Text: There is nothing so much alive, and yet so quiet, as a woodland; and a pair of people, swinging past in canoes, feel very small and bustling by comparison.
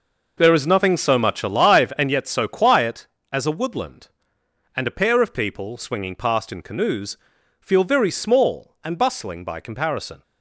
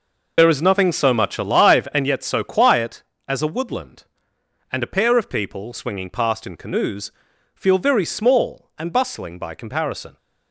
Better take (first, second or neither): first